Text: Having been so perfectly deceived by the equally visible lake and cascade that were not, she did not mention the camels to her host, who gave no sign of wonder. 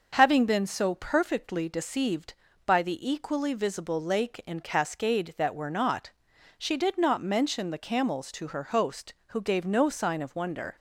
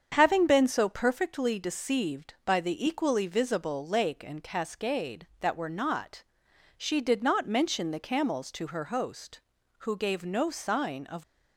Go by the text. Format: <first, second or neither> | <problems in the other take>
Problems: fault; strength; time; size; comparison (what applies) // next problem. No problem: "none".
first | starts louder than the rest; strong; until 1.1 s; 7.5 dB // stops before "wonder"; at 11.2 s